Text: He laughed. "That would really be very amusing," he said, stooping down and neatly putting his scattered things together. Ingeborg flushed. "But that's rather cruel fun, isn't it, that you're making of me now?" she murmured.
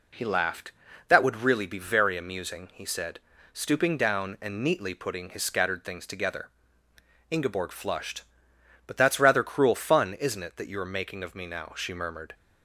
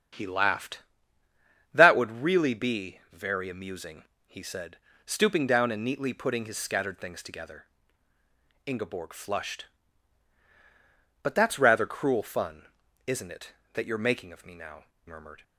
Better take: first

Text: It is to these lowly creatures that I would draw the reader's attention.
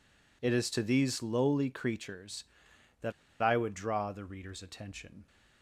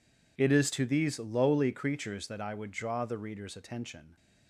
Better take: second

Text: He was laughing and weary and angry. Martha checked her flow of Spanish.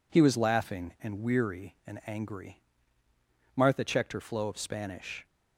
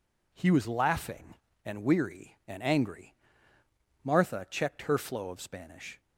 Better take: neither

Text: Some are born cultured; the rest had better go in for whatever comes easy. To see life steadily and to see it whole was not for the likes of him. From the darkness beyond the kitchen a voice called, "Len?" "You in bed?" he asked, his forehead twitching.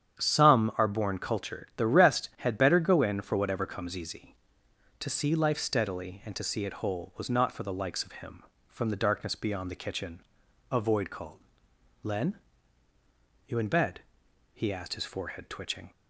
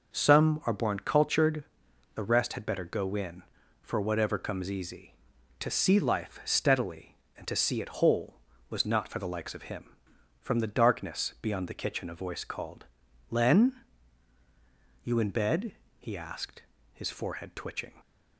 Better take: second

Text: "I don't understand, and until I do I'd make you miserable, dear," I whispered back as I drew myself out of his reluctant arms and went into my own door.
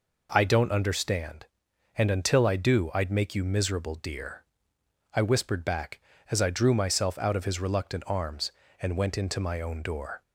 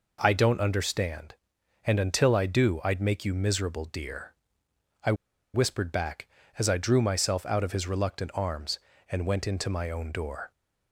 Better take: first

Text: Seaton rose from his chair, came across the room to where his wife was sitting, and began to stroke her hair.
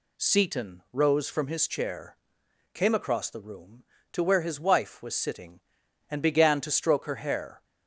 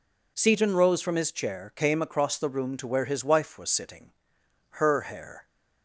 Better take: first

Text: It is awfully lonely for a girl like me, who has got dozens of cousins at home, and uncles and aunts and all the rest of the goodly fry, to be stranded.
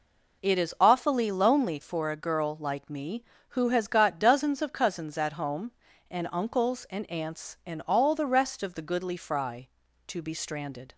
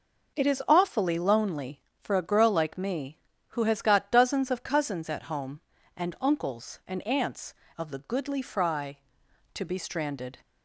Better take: first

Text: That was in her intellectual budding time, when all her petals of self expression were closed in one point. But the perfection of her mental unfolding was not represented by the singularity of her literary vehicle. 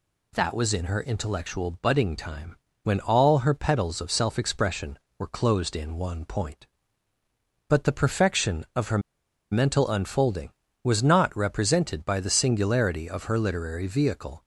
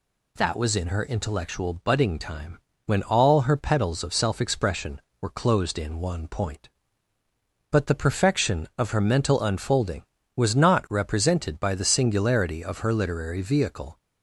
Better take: second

